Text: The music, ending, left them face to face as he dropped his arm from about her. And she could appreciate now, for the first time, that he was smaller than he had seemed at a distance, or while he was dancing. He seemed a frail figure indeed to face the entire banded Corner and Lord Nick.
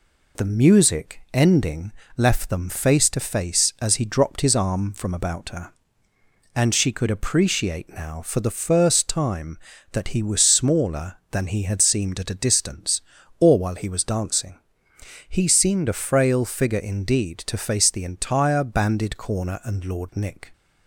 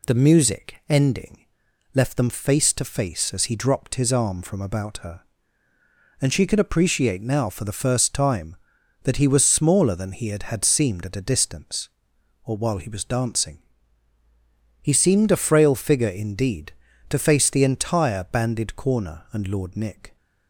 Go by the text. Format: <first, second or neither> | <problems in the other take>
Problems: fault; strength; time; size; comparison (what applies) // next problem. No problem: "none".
first | says "had" twice; at 10.4 s